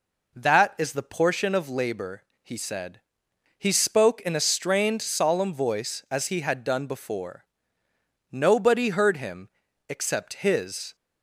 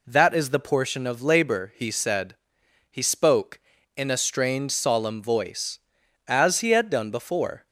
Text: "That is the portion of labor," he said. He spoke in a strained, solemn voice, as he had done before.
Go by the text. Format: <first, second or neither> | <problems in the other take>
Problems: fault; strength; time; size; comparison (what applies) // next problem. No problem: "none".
second | goes on to say "Nobody heard him except his"; strong; from 8.3 s on; 2.6 s long